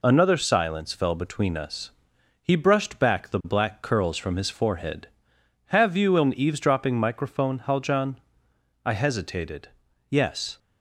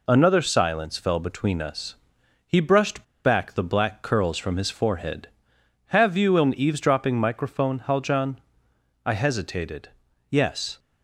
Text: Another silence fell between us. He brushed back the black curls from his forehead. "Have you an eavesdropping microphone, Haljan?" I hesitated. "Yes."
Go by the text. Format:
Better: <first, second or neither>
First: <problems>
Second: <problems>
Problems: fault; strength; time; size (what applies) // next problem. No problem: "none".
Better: first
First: none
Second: pauses between "brushed" and "back"; slight; at 3.0 s; 0.21 s long